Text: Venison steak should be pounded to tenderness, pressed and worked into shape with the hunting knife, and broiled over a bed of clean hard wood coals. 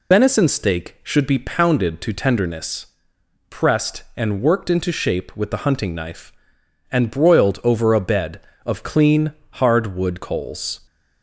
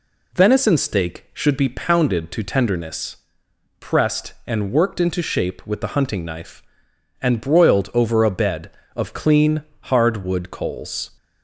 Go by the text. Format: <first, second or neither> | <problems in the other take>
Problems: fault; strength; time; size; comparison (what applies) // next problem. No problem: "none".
second | loses the start of "Venison"; at 0.1 s; 60 ms // pauses between "clean" and "hard"; slight; at 9.3 s; 0.20 s long; slight in the second